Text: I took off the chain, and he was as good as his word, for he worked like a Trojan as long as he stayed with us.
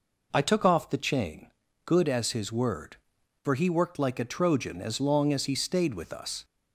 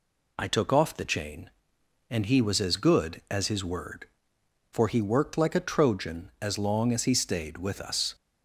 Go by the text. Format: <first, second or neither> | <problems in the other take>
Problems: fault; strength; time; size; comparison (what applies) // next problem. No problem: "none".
second | skips "and he was as"; at 1.6 s